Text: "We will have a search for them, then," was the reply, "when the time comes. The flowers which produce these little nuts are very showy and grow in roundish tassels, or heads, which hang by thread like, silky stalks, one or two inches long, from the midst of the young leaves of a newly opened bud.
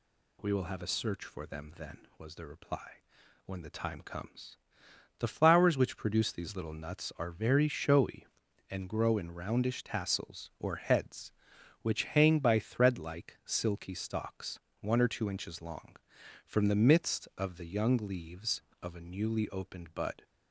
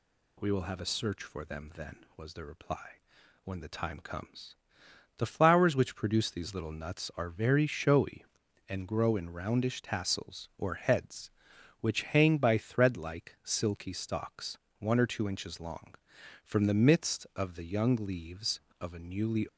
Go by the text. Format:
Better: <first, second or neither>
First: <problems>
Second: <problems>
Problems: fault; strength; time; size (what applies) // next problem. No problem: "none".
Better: first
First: none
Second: stops before "opened bud"; at 19.4 s